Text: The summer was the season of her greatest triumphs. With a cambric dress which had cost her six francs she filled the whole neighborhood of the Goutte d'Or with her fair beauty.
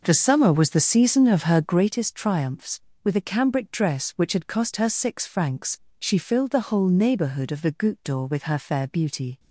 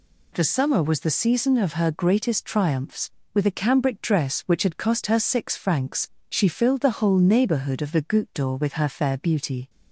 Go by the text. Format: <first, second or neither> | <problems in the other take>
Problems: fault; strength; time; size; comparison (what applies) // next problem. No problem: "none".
second | starts louder than the rest; noticeable; until 2.0 s; 5.5 dB // pauses between "francs" and "she"; slight; at 5.7 s; 0.20 s long; slight in the second